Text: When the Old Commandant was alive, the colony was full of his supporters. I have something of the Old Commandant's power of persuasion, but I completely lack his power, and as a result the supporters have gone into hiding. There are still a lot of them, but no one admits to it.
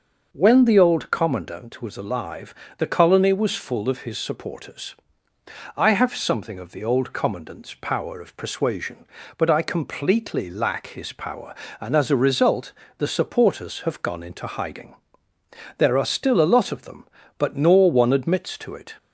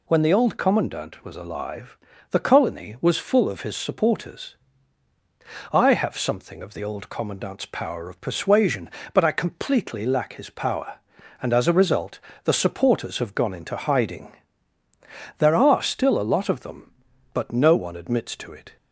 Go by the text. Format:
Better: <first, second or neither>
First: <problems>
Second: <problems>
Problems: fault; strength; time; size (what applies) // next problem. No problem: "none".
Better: second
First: starts louder than the rest; noticeable; until 1.3 s; 6 dB // pauses between "result" and "the"; slight; at 12.7 s; 0.28 s long // says "nor" for "no"; at 17.5 s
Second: pauses between "result" and "the"; slight; at 12.2 s; 0.24 s long